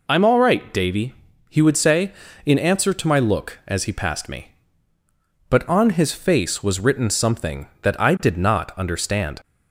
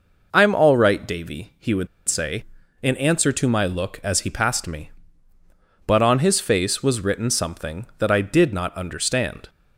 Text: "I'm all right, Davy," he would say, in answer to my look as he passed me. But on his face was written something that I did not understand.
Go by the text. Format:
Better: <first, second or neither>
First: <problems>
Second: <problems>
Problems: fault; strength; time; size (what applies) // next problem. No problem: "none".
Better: first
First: none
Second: pauses between "would" and "say"; slight; at 1.8 s; 0.21 s long